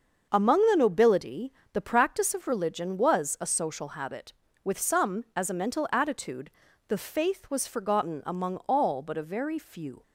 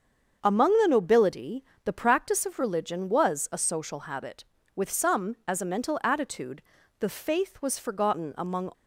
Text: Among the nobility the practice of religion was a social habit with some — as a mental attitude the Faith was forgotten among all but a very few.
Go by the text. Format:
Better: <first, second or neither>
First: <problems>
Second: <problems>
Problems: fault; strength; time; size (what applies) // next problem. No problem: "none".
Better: first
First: starts louder than the rest; until 1.3 s; 6.5 dB // pauses between "nobility" and "the"; slight; at 1.5 s; 0.18 s long // pauses between "attitude" and "the"; at 6.5 s; 0.38 s long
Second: starts louder than the rest; until 1.4 s; 7 dB // pauses between "nobility" and "the"; slight; at 1.6 s; 0.18 s long // pauses between "attitude" and "the"; at 6.6 s; 0.38 s long // stops before "all but a very few"; at 8.7 s